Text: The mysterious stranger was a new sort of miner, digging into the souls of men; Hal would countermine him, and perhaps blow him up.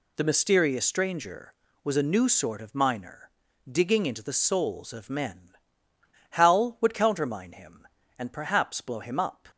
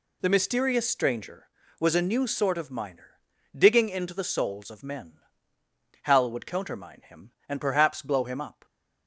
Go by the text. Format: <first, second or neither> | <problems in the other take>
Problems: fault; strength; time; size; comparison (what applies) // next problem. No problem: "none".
neither | none